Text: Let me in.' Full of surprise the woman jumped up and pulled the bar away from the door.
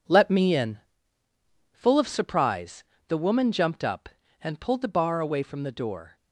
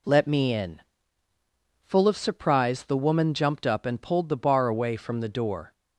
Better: second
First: gets quieter; strong; throughout; 8.5 dB // pauses between "surprise" and "the"; slight; at 2.8 s; 0.24 s long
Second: none

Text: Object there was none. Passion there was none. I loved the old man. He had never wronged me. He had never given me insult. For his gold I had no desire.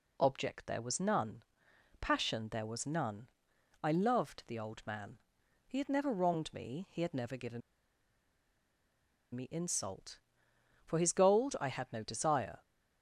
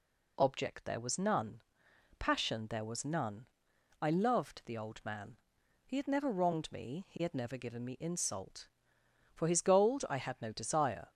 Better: second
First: pauses between "given" and "me"; strong; at 7.6 s; 1.7 s long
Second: none

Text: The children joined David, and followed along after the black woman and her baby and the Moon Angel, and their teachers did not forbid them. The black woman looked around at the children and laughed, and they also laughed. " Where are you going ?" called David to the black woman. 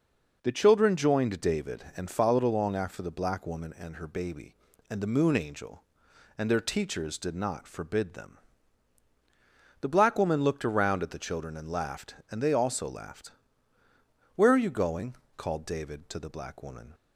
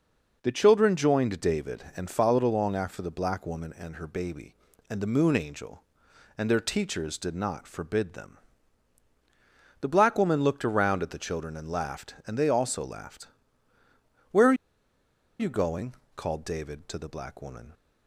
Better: first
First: none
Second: pauses between "are" and "you"; noticeable; at 14.5 s; 0.86 s long

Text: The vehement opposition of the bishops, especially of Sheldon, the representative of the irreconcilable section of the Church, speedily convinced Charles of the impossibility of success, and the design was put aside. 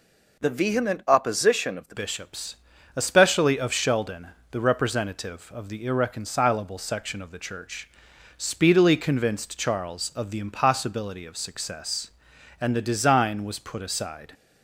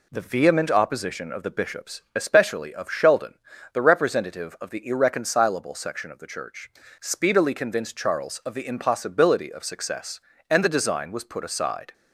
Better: second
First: changes voice at "bishops"; from 1.9 s on; 12.4 s long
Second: none

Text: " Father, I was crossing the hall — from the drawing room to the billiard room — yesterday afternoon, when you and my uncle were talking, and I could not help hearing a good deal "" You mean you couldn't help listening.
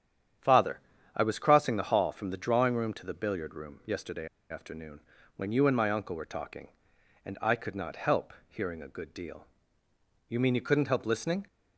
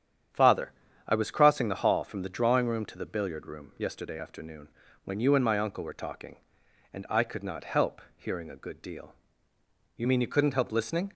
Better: second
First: starts louder than the rest; strong; until 1.7 s; 9.5 dB // pauses between "yesterday" and "afternoon"; slight; at 4.2 s; 0.24 s long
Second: starts louder than the rest; strong; until 1.6 s; 9.5 dB

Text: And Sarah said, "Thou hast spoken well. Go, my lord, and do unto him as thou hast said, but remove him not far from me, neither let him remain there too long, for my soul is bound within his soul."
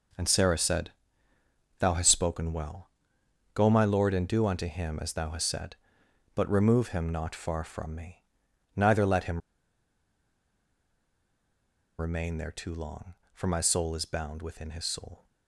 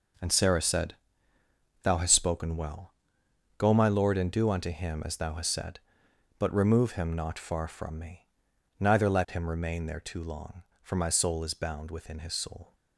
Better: second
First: pauses between "him" and "remain"; strong; at 9.4 s; 2.5 s long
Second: none

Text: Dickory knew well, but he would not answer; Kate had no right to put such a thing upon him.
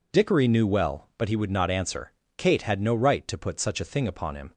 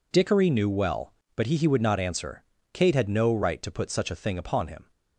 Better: first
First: none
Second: says "he" twice; at 1.5 s

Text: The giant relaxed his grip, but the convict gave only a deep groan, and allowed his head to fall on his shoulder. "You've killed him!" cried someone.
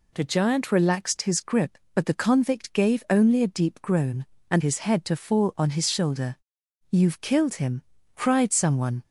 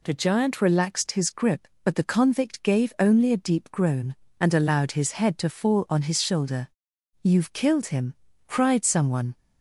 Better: second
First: skips "allowed"; at 4.6 s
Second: none

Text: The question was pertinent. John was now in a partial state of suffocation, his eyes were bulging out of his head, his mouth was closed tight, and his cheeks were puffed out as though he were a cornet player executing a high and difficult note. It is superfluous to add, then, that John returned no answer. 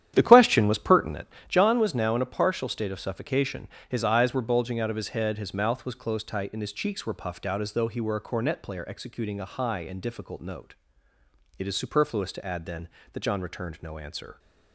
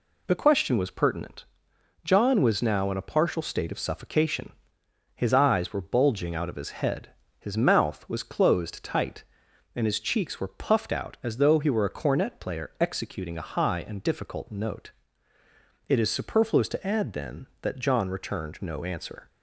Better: second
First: starts louder than the rest; strong; until 1.6 s; 10.5 dB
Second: none

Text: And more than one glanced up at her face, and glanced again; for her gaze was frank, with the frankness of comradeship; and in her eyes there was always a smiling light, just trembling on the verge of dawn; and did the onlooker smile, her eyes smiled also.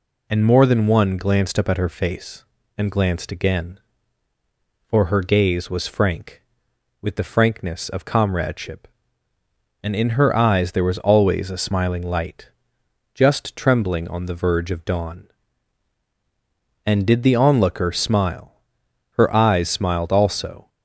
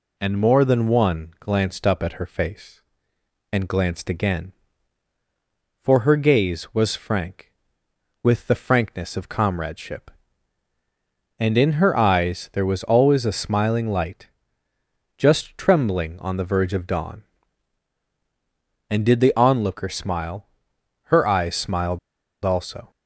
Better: first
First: none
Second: pauses between "smiled" and "also"; at 21.9 s; 0.45 s long

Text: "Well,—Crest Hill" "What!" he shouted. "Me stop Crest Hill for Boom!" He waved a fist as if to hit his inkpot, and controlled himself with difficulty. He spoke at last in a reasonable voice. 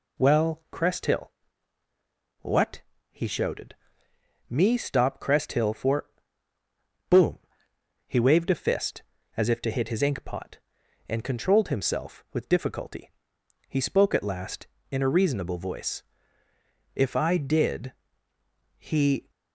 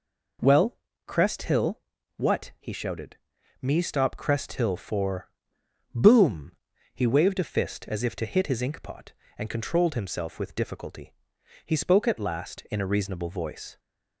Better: second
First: pauses between "Hill" and "What"; at 1.3 s; 1.1 s long // pauses between "for" and "Boom"; at 6.0 s; 1.0 s long // goes on to say "If I did he"; strong; from 17.0 s on; 2.3 s long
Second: pauses between "Hill" and "What"; slight; at 1.8 s; 0.34 s long // pauses between "for" and "Boom"; noticeable; at 5.2 s; 0.66 s long

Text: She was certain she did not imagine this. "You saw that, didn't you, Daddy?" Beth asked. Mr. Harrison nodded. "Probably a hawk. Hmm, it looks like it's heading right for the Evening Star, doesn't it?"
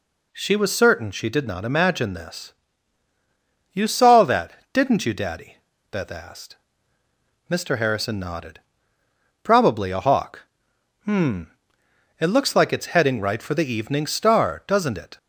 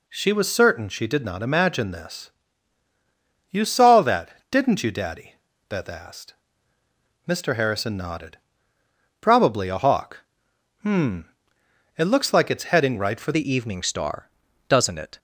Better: first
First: none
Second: changes voice at "the"; from 13.3 s on; 1.8 s long

